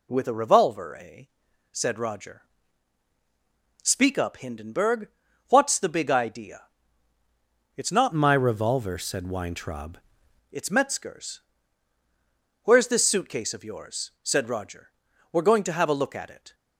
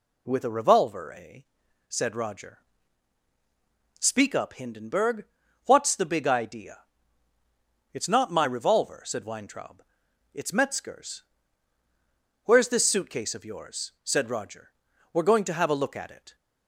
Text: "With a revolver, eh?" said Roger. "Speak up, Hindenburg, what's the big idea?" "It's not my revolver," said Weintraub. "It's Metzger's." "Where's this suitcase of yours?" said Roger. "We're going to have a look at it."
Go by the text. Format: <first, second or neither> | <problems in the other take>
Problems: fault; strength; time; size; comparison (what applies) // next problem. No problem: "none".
second | changes voice from "my" to "Weintraub"; from 8.1 to 9.9 s; 1.8 s long